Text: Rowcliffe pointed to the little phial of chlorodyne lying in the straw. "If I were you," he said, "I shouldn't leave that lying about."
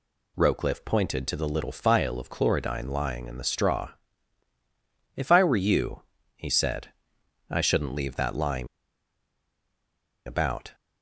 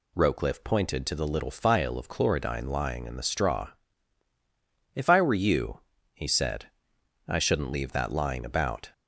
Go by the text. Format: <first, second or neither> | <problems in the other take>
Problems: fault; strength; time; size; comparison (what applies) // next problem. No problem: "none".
second | pauses between "lying" and "about"; strong; at 8.6 s; 1.5 s long